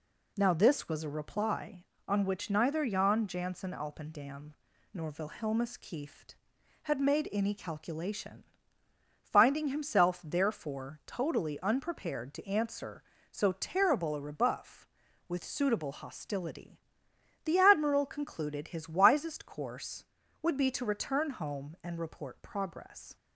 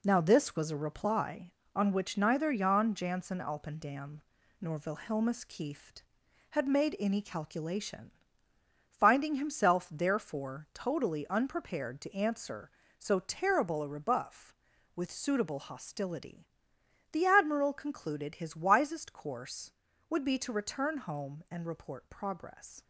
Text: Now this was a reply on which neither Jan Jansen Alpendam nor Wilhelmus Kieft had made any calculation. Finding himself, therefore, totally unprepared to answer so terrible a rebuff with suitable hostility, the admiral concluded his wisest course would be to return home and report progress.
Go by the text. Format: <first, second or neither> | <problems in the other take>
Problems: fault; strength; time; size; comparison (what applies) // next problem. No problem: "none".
first | gets quieter; throughout; 6 dB // pauses between "Alpendam" and "nor"; at 4.2 s; 0.38 s long; also in the first